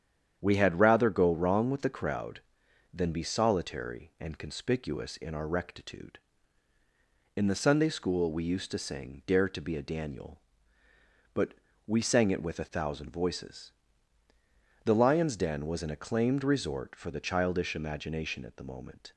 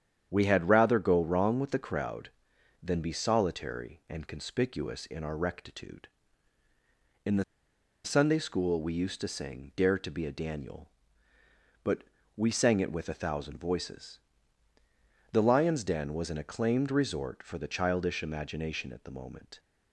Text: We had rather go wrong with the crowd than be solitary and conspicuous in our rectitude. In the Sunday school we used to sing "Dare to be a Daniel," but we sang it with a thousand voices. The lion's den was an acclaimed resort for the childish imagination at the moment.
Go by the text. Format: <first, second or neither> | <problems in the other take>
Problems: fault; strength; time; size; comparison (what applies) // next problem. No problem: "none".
first | starts louder than the rest; strong; until 1.3 s; 9 dB; strong in the first // pauses between "the" and "Sunday"; noticeable; at 7.4 s; 0.61 s long // pauses between "but" and "we"; slight; at 12.0 s; 0.32 s long; slight in the first